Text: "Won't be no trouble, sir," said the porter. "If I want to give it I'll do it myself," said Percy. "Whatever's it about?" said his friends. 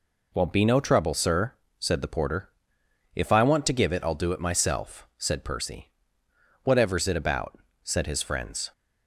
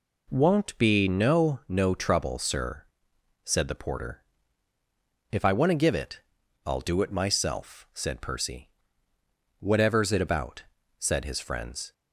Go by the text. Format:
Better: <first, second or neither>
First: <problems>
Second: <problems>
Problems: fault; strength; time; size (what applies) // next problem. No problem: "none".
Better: first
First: none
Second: says "no" twice; at 1.6 s // pauses between "it" and "I'll"; noticeable; at 6.2 s; 0.46 s long